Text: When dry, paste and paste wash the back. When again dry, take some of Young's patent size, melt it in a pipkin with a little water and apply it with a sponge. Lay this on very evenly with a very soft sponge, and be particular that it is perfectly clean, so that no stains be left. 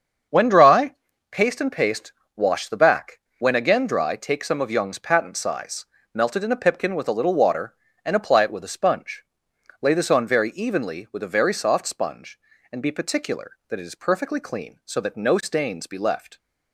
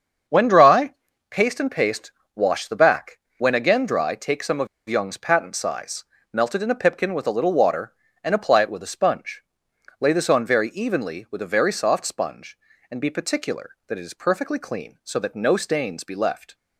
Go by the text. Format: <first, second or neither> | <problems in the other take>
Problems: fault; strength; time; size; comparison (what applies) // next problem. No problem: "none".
first | starts louder than the rest; until 1.6 s; 7 dB; also in the first // pauses between "paste" and "wash"; slight; at 2.1 s; 0.24 s long; slight in the first // pauses between "of" and "Young's"; slight; at 4.6 s; 0.21 s long